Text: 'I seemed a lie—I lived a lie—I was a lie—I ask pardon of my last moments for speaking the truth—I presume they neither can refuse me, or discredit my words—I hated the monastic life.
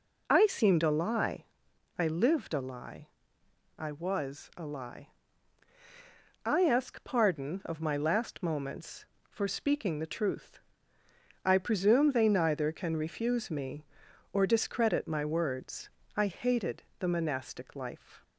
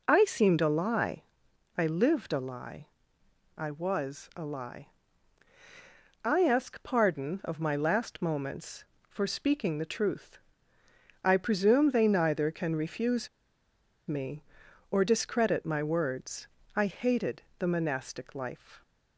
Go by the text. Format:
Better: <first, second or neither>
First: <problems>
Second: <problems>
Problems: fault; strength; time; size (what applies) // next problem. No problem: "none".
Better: first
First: pauses between "hated" and "the"; slight; at 16.8 s; 0.18 s long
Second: pauses between "refuse" and "me"; noticeable; at 13.2 s; 0.79 s long // pauses between "hated" and "the"; slight; at 17.4 s; 0.18 s long